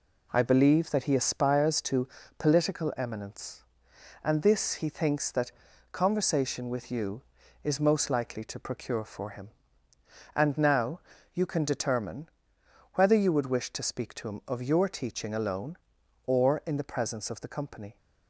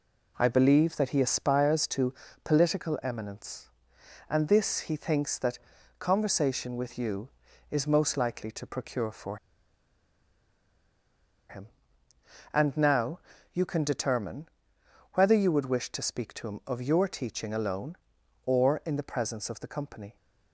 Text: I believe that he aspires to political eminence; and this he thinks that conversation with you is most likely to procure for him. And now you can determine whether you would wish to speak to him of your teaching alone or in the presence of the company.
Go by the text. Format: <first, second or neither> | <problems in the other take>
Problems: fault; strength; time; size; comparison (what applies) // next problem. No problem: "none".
first | pauses between "to" and "political"; slight; at 2.1 s; 0.30 s long; slight in the first // pauses between "that" and "conversation"; at 5.5 s; 0.40 s long; also in the first // pauses between "for" and "him"; strong; at 9.3 s; 2.1 s long // pauses between "now" and "you"; slight; at 13.1 s; 0.34 s long; slight in the first // pauses between "determine" and "whether"; noticeable; at 14.4 s; 0.66 s long; noticeable in the first